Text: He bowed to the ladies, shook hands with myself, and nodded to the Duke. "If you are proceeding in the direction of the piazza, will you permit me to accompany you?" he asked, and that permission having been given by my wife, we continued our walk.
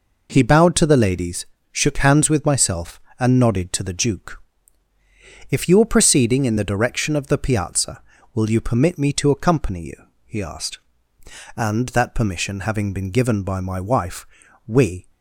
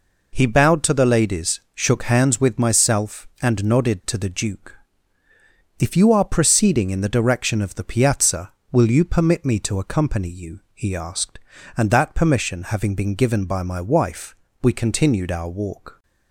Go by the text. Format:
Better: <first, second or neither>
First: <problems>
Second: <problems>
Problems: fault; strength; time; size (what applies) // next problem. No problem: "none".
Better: second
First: stops before "continued our walk"; at 15.0 s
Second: none